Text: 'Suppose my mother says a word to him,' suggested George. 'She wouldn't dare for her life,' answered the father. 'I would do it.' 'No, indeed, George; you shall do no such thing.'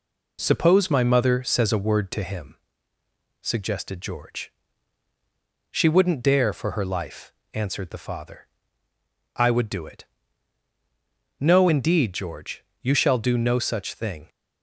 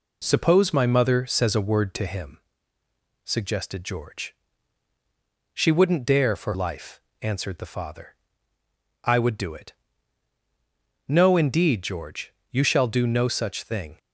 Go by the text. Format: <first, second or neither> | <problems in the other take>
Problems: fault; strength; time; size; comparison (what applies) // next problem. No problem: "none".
first | skips "her"; at 6.5 s